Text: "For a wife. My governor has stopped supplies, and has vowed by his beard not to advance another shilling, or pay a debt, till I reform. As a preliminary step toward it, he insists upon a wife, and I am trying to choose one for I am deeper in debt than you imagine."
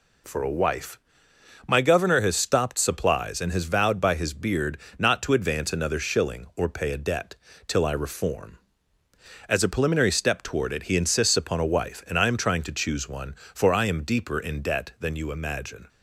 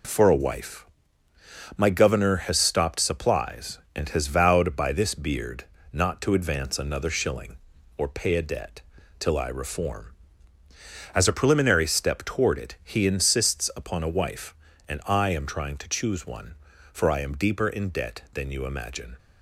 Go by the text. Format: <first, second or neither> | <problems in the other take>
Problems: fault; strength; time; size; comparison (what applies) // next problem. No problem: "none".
first | says "this" for "his"; at 4.9 s // pauses between "beard" and "not"; slight; at 5.6 s; 0.28 s long; slight in the first